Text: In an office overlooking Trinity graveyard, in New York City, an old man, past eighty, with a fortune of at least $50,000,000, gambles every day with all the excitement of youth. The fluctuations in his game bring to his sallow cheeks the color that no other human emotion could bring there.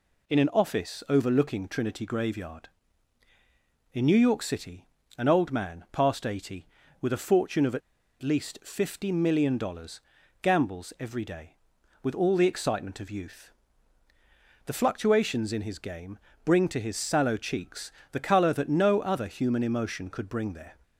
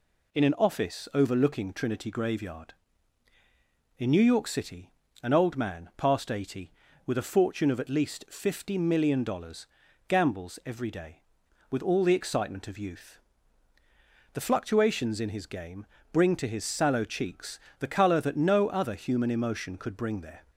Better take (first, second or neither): second